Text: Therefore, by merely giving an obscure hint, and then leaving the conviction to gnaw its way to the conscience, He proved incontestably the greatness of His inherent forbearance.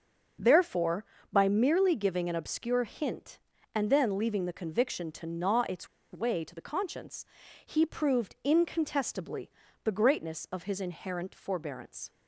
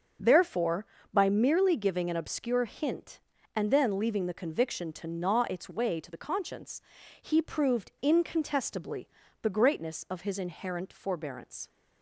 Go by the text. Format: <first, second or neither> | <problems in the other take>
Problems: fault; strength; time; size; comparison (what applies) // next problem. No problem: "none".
second | starts louder than the rest; noticeable; until 1.7 s; 6 dB; noticeable in the second // pauses between "its" and "way"; slight; at 5.8 s; 0.25 s long // pauses between "incontestably" and "the"; slight; at 9.5 s; 0.34 s long; slight in the second